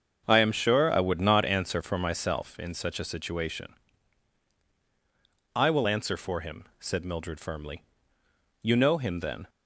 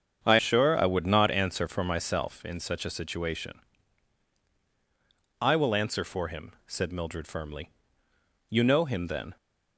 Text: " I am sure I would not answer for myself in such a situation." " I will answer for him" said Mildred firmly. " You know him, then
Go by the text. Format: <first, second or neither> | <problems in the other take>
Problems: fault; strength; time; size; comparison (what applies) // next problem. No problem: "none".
first | starts louder than the rest; strong; until 1.2 s; 9 dB; strong in the first // skips "am"; at 0.3 s // pauses between "him" and "said"; slight; at 6.5 s; 0.16 s long; slight in the first